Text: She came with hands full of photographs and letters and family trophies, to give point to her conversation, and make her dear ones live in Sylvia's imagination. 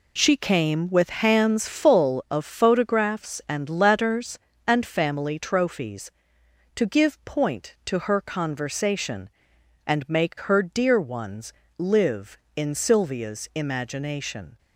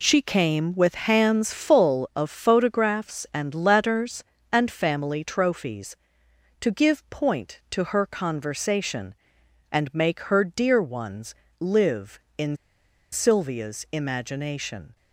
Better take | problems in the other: first | pauses between "ones" and "live"; slight; at 11.3 s; 0.24 s long; slight in the first // pauses between "in" and "Sylvia's"; noticeable; at 12.5 s; 0.56 s long

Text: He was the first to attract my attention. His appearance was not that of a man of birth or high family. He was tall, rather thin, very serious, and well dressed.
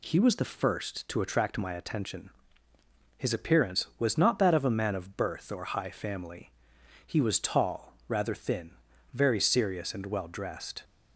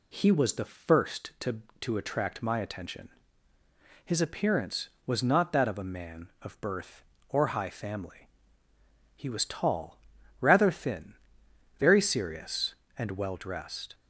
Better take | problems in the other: first | says "to" twice; at 1.8 s

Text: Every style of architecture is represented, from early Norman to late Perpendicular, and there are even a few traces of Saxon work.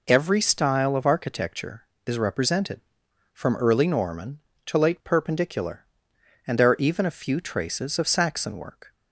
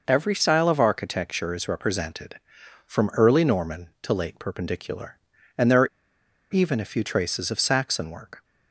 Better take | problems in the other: first | pauses between "are" and "even"; noticeable; at 5.8 s; 0.66 s long

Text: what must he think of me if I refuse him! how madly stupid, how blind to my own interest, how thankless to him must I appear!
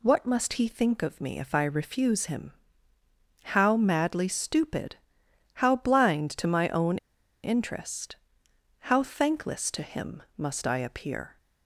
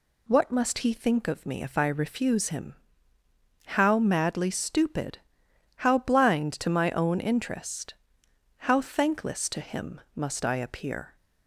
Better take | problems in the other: second | pauses between "own" and "interest"; noticeable; at 6.9 s; 0.46 s long // pauses between "him" and "must"; slight; at 10.2 s; 0.16 s long; slight in the second

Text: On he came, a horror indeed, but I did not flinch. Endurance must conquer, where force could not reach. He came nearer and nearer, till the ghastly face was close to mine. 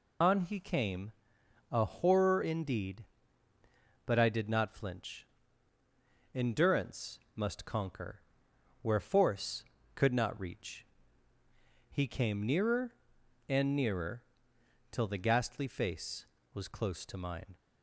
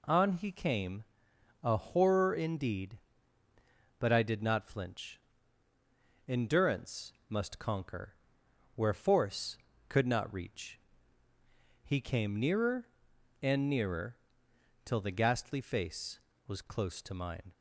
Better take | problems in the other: second | loses the start of "On"; at 0.2 s; 85 ms // pauses between "Endurance" and "must"; slight; at 7.1 s; 0.16 s long; slight in the second

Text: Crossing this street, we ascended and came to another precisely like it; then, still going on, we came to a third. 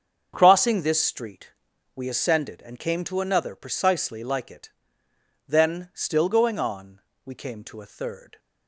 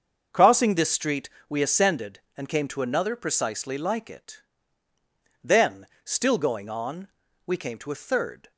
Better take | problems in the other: neither | starts louder than the rest; the same in both

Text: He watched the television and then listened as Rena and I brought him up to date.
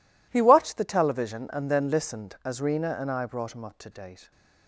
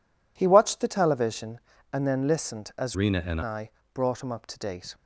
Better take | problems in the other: first | changes voice from "Rena" to "and"; from 2.9 to 3.4 s; 0.5 s long // pauses between "I" and "brought"; slight; at 3.7 s; 0.24 s long

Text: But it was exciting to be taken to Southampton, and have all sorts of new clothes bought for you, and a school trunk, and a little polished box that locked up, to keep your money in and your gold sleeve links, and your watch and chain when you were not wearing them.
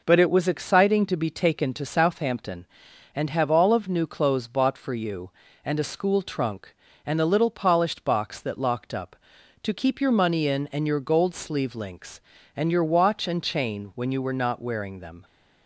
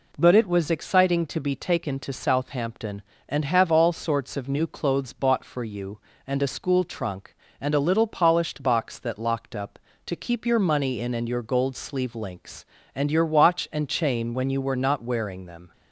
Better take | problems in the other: second | skips "sorts"; at 3.7 s

